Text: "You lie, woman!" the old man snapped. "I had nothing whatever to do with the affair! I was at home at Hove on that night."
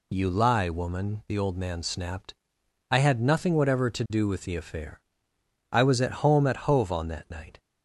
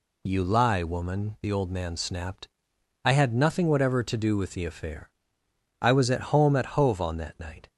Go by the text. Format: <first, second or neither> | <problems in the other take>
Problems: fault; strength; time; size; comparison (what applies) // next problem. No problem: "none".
neither | none